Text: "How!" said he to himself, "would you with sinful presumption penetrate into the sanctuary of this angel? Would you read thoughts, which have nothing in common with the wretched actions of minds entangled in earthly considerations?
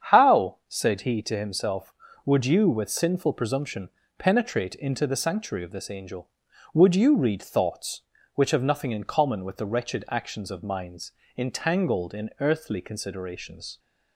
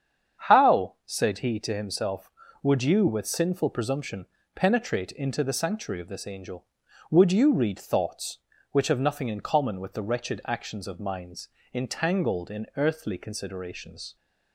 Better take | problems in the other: neither | starts louder than the rest; strong; the same in both // pauses between "presumption" and "penetrate"; slight; the same in both // pauses between "minds" and "entangled"; slight; the same in both

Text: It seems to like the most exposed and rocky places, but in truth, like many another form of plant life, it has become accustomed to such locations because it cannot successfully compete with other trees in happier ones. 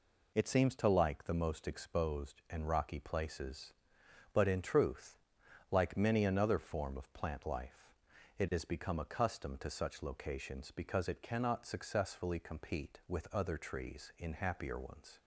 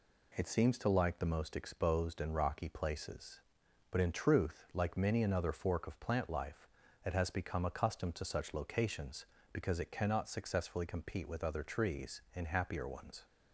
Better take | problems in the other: first | says "fork" for "form"; at 5.5 s

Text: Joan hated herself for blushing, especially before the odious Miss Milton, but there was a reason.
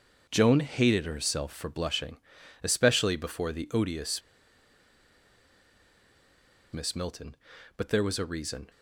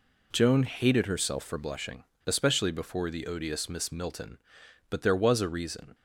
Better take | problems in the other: second | starts louder than the rest; until 1.3 s; 6.5 dB // pauses between "odious" and "Miss"; strong; at 4.2 s; 2.5 s long

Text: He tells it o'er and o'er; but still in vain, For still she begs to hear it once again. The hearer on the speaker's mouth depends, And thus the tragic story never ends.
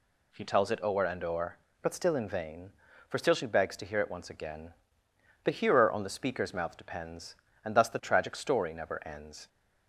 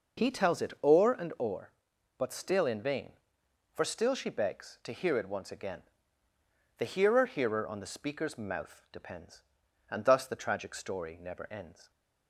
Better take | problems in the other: first | says "hearer" twice; at 7.2 s

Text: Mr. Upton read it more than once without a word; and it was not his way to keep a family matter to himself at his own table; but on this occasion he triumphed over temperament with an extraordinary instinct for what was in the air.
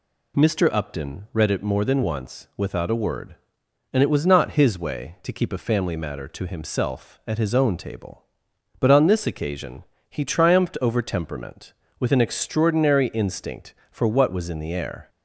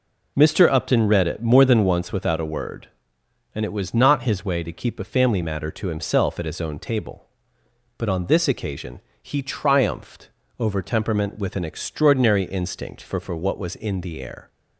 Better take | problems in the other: first | pauses between "occasion" and "he"; slight; at 8.9 s; 0.24 s long; slight in the first // pauses between "triumphed" and "over"; slight; at 10.2 s; 0.30 s long // says "for" twice; at 13.2 s

